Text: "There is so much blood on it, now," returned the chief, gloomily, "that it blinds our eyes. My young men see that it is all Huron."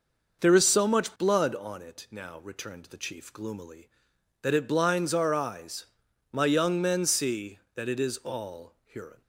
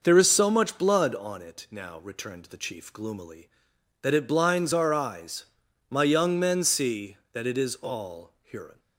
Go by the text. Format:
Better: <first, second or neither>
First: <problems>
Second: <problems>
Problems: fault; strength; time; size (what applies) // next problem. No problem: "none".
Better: neither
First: none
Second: none